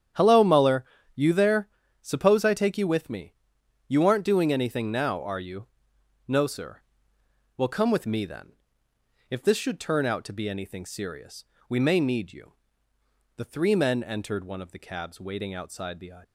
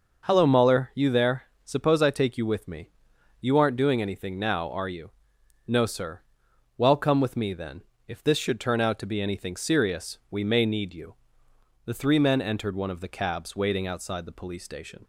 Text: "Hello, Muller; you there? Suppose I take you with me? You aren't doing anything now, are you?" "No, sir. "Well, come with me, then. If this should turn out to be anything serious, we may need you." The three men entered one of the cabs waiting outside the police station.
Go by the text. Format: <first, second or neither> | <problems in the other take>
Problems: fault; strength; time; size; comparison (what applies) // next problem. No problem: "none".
second | starts louder than the rest; strong; until 1.4 s; 9.5 dB // stops before "police station"; at 16.2 s